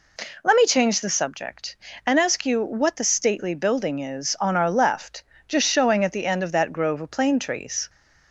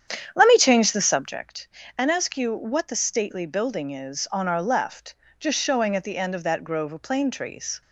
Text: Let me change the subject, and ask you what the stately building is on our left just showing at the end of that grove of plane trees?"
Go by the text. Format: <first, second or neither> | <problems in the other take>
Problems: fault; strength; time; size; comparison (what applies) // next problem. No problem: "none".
first | starts louder than the rest; strong; until 1.5 s; 9 dB // pauses between "left" and "just"; slight; at 5.1 s; 0.24 s long; slight in the first